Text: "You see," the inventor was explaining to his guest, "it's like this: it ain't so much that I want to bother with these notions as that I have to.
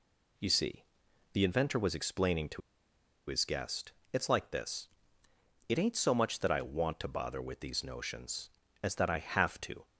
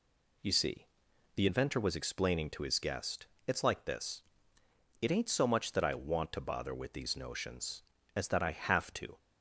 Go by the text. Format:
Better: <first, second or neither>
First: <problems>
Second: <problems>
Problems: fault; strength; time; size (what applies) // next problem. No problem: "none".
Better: second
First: pauses between "to" and "his"; noticeable; at 2.6 s; 0.68 s long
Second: none